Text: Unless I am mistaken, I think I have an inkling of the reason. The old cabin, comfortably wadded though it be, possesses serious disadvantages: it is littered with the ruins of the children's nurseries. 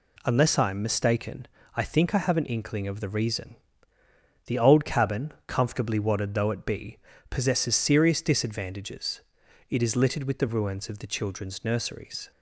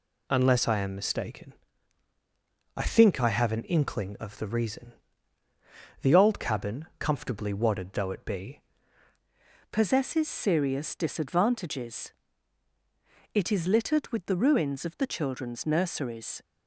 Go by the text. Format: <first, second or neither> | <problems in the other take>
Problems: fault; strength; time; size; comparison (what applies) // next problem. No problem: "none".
first | changes voice at "possesses"; from 9.7 s on; 6.7 s long